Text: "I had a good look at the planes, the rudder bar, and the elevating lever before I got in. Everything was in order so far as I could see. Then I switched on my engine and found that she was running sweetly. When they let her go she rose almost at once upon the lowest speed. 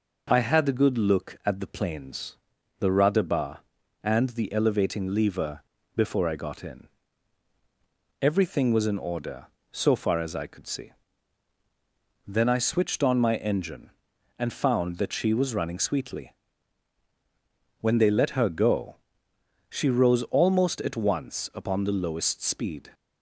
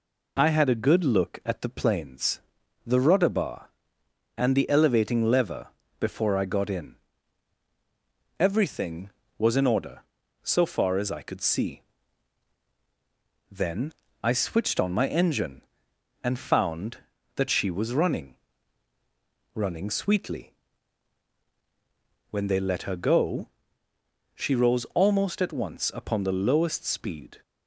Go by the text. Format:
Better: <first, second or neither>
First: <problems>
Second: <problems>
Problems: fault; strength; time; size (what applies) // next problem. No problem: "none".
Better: first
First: pauses between "lever" and "before"; slight; at 5.6 s; 0.34 s long // pauses between "go" and "she"; noticeable; at 18.9 s; 0.74 s long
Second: pauses between "lever" and "before"; slight; at 5.6 s; 0.28 s long // pauses between "Then" and "I"; slight; at 13.9 s; 0.30 s long // says "running" twice; at 19.5 s // pauses between "go" and "she"; noticeable; at 23.4 s; 0.88 s long